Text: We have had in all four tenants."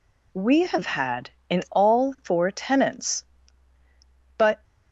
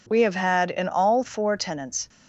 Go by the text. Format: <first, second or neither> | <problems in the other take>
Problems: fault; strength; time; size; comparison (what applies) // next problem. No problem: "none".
second | goes on to say "But"; slight; from 4.3 s on; 0.26 s long